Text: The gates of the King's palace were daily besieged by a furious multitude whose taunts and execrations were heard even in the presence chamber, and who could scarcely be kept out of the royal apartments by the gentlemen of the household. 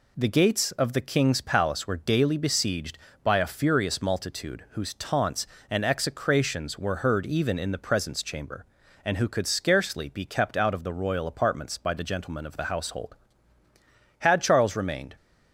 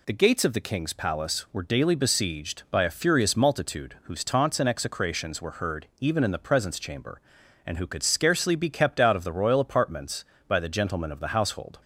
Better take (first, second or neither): second